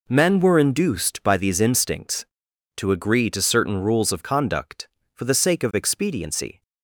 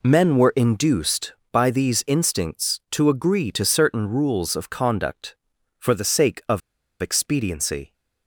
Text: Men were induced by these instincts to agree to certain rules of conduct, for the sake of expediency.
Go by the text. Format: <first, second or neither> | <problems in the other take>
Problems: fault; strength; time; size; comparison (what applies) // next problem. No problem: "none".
first | pauses between "of" and "expediency"; at 6.6 s; 0.42 s long